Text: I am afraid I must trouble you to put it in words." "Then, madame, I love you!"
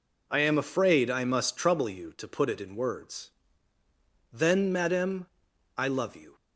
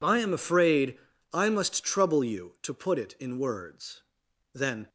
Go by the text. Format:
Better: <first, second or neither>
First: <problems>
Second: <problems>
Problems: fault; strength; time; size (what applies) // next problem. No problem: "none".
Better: first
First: none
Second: pauses between "afraid" and "I"; slight; at 0.9 s; 0.36 s long // stops before "madame I love you"; at 4.8 s